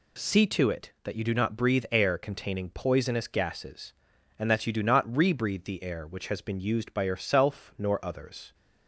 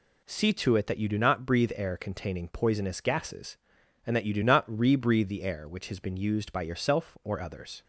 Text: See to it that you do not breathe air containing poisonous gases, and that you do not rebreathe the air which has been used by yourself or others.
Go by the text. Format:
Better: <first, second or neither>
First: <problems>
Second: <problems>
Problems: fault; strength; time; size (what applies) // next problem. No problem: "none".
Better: second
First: says "nor" for "or"; at 7.7 s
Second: none